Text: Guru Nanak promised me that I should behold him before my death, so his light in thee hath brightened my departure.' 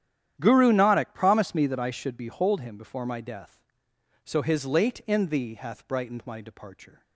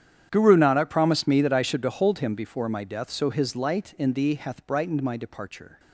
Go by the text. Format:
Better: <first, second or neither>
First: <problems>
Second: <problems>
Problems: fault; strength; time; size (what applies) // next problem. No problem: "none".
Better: second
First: starts louder than the rest; strong; until 1.4 s; 10.5 dB // says "late" for "light"; at 4.6 s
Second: starts louder than the rest; strong; until 1.3 s; 9.5 dB